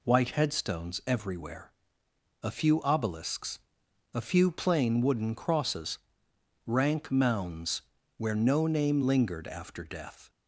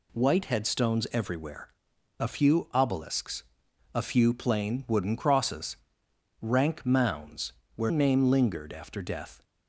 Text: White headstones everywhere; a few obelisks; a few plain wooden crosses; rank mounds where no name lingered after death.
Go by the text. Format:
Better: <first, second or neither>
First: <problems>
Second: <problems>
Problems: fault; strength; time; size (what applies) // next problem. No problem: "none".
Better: first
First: pauses between "mounds" and "where"; slight; at 7.8 s; 0.34 s long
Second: pauses between "mounds" and "where"; slight; at 7.5 s; 0.24 s long // skips "no"; at 7.8 s